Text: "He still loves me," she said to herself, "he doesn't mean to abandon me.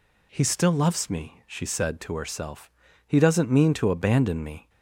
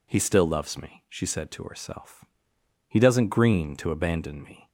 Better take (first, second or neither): first